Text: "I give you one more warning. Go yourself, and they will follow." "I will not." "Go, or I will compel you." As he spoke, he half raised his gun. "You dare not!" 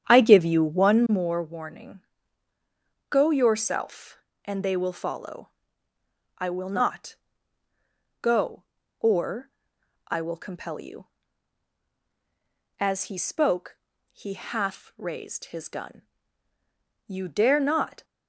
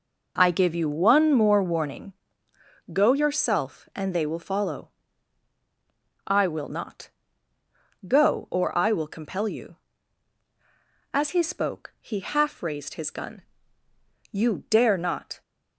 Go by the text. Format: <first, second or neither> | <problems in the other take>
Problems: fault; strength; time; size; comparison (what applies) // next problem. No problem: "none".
second | starts louder than the rest; strong; until 1.2 s; 9 dB // pauses between "or" and "I"; noticeable; at 9.5 s; 0.56 s long